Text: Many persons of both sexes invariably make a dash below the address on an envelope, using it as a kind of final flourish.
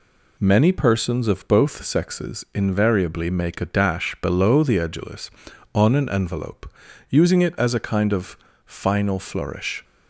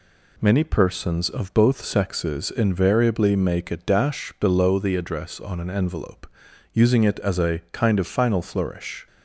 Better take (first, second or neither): second